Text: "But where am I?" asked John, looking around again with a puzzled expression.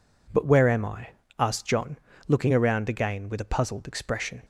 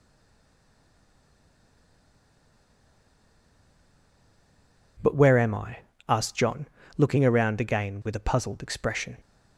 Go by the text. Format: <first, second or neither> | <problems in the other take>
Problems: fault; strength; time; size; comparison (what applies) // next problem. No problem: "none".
first | stays silent before the first word; strong; until 4.9 s; 4.9 s long